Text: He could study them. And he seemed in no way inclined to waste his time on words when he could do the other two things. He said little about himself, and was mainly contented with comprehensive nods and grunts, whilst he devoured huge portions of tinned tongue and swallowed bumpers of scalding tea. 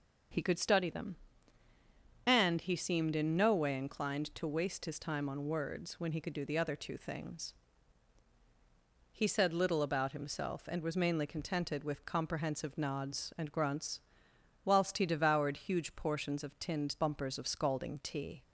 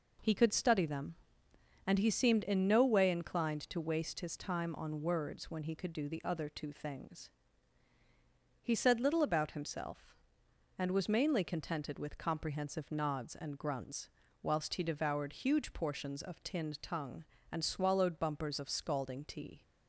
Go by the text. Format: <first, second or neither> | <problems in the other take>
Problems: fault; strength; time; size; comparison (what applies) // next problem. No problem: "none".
second | starts louder than the rest; until 2.4 s; 6.5 dB // skips "tongue and swallowed"; at 16.9 s